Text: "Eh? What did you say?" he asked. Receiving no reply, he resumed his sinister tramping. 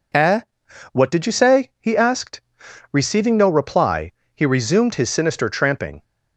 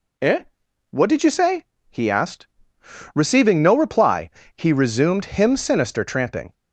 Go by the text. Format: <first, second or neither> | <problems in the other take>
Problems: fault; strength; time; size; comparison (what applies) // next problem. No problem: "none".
first | says "him" for "his"; at 5.2 s